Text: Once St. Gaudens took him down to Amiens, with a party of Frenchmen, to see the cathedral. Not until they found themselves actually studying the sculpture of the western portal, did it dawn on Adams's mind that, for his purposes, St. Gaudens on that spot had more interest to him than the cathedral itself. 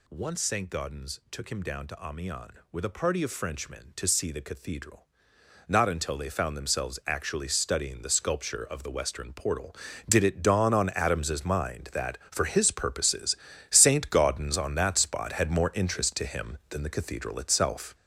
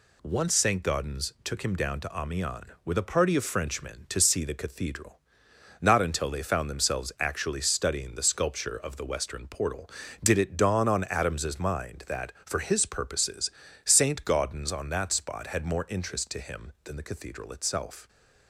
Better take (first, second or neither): second